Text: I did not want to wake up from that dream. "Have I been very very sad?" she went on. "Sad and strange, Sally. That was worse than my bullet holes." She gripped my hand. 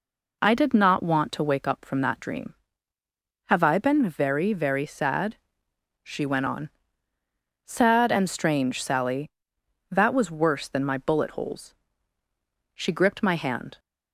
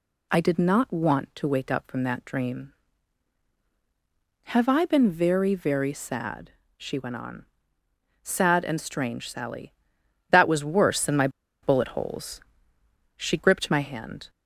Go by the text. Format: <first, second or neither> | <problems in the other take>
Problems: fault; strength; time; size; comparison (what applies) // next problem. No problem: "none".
first | pauses between "my" and "bullet"; slight; at 11.2 s; 0.34 s long